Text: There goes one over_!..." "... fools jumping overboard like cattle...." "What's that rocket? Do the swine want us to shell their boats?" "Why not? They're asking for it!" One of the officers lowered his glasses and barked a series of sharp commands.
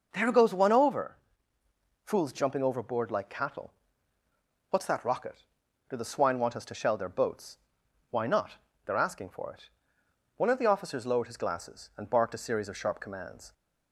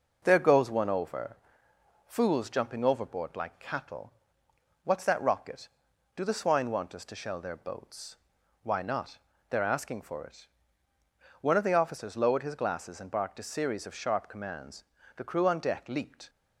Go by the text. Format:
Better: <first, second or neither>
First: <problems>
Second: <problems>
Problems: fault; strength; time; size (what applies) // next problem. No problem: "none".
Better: first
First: none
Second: starts louder than the rest; until 1.2 s; 6.5 dB // goes on to say "The crew on deck leaped"; noticeable; from 15.1 s on; 1.1 s long